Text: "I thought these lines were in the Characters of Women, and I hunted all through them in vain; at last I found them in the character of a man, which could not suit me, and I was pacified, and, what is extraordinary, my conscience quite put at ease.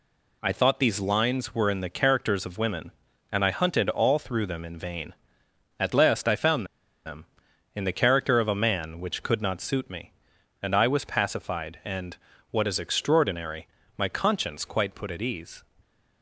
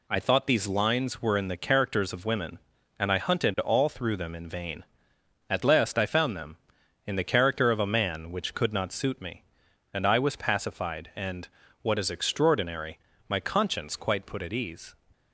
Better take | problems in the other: second | pauses between "found" and "them"; at 6.6 s; 0.40 s long

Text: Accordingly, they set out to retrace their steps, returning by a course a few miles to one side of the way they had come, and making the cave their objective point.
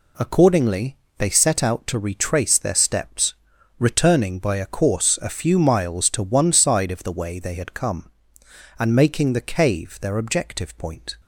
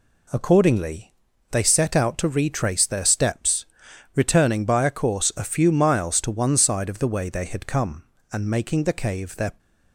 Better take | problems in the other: first | stops before "objective point"; at 9.5 s

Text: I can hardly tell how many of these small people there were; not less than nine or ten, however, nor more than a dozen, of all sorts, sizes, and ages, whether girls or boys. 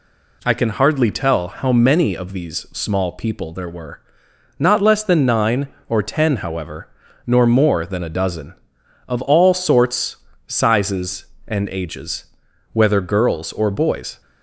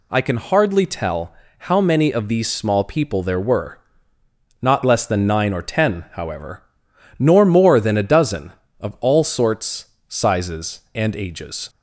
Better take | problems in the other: first | pauses between "tell" and "how"; slight; at 1.3 s; 0.26 s long // stops before "whether girls or boys"; at 11.6 s

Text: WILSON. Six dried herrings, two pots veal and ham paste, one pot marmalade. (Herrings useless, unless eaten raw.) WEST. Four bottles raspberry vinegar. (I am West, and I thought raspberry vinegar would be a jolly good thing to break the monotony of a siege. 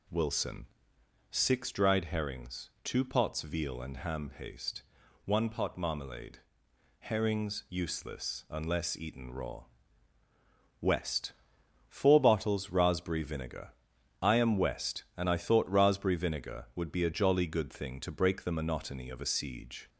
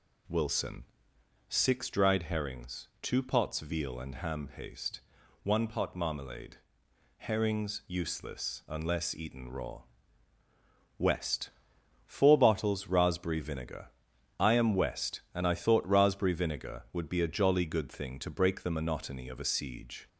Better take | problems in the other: neither | none

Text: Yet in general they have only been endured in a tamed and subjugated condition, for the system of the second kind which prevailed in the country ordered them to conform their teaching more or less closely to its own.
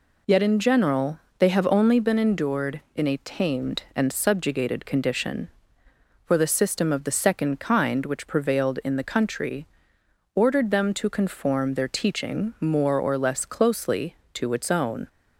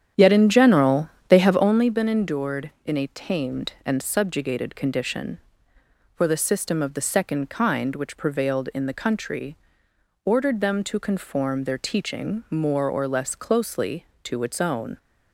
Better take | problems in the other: first | starts louder than the rest; strong; until 1.8 s; 9.5 dB // pauses between "general" and "they"; slight; at 1.0 s; 0.20 s long; slight in the first // pauses between "country" and "ordered"; noticeable; at 9.5 s; 0.68 s long; noticeable in the first

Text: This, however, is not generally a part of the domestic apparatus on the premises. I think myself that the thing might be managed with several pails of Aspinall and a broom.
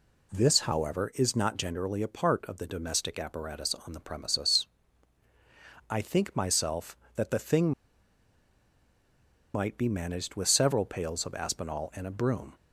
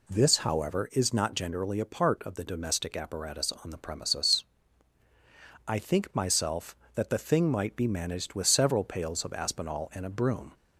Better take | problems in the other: second | pauses between "thing" and "might"; strong; at 7.7 s; 1.8 s long

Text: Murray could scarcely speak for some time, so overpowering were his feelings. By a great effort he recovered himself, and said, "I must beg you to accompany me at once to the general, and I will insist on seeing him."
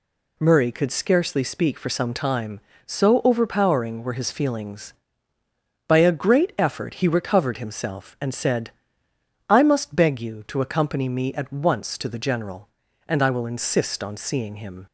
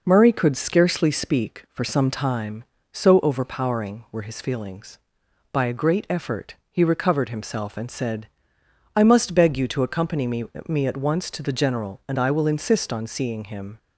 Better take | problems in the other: first | says "me" twice; at 10.6 s

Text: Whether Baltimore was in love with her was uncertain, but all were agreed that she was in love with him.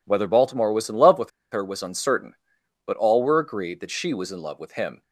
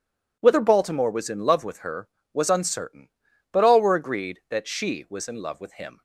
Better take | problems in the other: second | pauses between "with" and "her"; slight; at 1.3 s; 0.21 s long

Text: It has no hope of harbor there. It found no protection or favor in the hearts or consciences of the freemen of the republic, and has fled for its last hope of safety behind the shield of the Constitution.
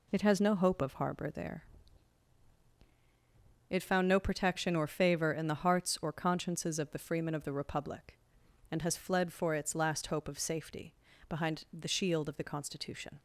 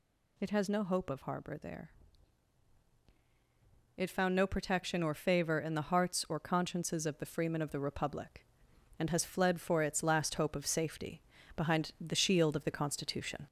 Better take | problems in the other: first | gets louder; slight; throughout; 2.5 dB // pauses between "safety" and "behind"; slight; at 11.2 s; 0.34 s long; slight in the first

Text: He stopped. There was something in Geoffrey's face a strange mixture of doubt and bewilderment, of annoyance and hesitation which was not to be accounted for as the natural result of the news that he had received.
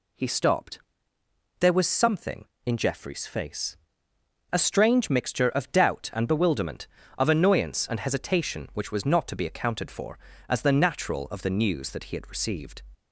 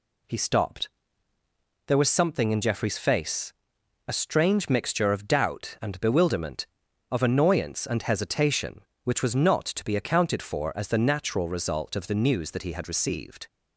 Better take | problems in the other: second | pauses between "face" and "a"; noticeable; at 3.7 s; 0.76 s long; noticeable in the second // skips "result"; at 11.2 s

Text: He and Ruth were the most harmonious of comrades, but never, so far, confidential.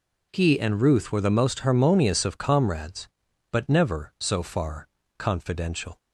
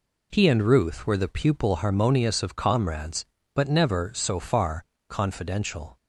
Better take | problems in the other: first | says "pupil" for "most"; at 1.2 s

